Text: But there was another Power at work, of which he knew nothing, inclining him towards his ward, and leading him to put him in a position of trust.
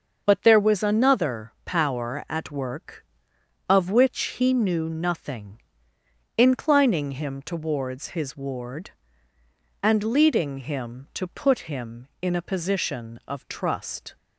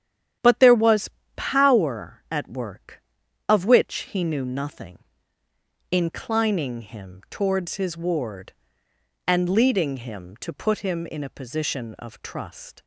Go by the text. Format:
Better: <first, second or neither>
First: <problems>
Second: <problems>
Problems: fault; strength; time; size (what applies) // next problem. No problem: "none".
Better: first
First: starts louder than the rest; until 1.2 s; 6.5 dB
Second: starts louder than the rest; strong; until 1.6 s; 9.5 dB // skips "another"; at 1.2 s